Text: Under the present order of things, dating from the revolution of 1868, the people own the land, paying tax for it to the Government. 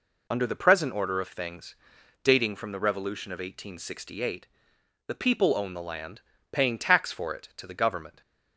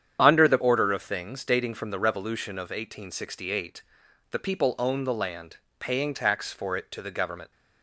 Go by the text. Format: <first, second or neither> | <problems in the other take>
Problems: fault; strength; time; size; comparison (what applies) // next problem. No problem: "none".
first | starts louder than the rest; strong; until 1.2 s; 8.5 dB // skips "present"; at 0.5 s